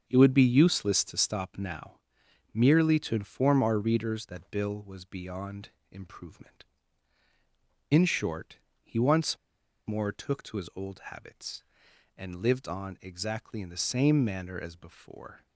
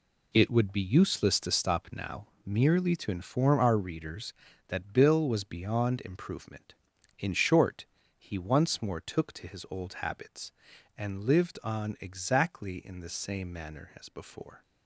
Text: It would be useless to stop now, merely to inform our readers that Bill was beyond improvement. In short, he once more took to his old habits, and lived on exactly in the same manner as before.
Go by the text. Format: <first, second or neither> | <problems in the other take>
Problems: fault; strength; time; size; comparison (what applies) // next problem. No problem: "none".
second | starts louder than the rest; until 1.0 s; 7 dB // pauses between "beyond" and "improvement"; slight; at 5.7 s; 0.20 s long // pauses between "once" and "more"; noticeable; at 9.3 s; 0.50 s long